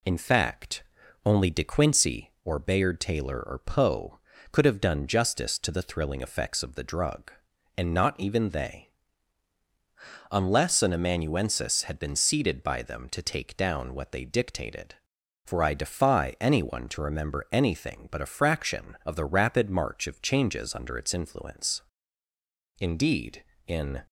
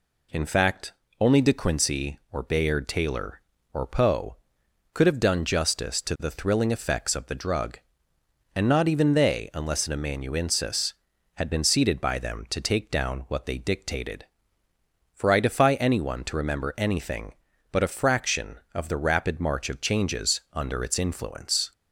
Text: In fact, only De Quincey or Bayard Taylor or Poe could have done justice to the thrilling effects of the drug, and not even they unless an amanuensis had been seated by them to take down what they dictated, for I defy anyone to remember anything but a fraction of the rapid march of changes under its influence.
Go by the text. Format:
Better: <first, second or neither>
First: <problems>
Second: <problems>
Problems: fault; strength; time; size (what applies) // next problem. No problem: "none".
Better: second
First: pauses between "they" and "unless"; strong; at 8.8 s; 1.4 s long // goes on to say "Indeed in"; noticeable; from 22.7 s on; 1.2 s long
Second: none